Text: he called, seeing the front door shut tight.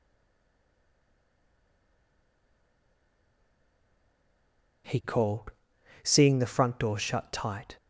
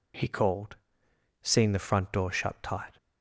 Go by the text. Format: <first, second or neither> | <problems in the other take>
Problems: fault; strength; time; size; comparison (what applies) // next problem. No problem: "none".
second | stays silent before the first word; strong; until 4.8 s; 4.8 s long